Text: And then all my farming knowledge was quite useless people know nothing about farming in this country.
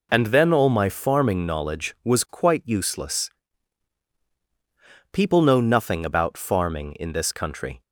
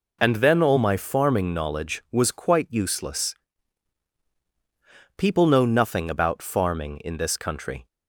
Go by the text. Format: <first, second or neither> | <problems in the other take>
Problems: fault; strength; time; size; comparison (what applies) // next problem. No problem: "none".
neither | pauses between "useless" and "people"; strong; the same in both